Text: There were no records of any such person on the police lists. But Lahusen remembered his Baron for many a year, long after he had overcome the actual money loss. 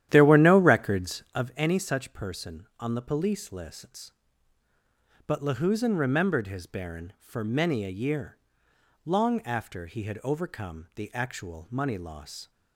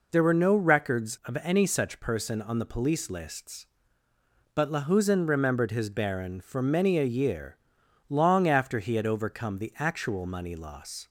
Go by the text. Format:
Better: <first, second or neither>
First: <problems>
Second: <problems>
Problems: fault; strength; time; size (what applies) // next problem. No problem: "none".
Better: second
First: starts louder than the rest; strong; until 1.5 s; 11.5 dB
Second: none